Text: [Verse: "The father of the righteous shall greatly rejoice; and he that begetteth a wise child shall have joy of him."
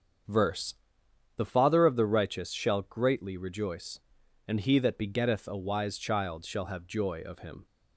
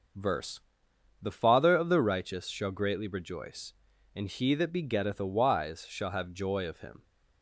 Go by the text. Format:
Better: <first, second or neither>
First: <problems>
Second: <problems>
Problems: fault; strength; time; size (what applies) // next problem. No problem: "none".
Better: first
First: starts louder than the rest; strong; until 1.9 s; 7.5 dB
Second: starts louder than the rest; until 1.7 s; 6.5 dB // skips "child"; at 5.8 s